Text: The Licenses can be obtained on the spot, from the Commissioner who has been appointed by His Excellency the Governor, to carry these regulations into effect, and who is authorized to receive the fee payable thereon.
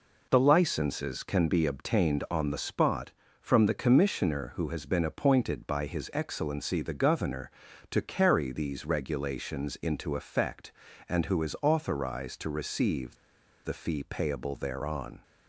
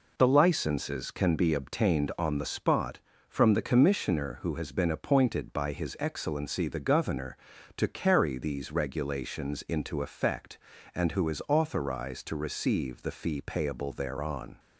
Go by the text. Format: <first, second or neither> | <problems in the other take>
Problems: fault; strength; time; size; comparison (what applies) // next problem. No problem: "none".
second | pauses between "receive" and "the"; noticeable; at 13.1 s; 0.48 s long